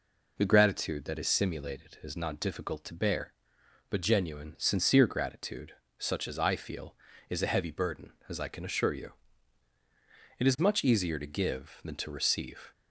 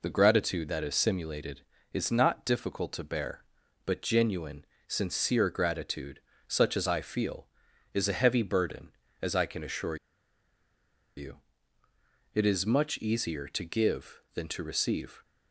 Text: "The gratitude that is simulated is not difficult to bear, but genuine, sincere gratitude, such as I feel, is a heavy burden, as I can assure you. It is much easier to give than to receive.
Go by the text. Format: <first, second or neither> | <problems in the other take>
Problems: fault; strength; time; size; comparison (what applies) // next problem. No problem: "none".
first | pauses between "assure" and "you"; at 9.9 s; 1.2 s long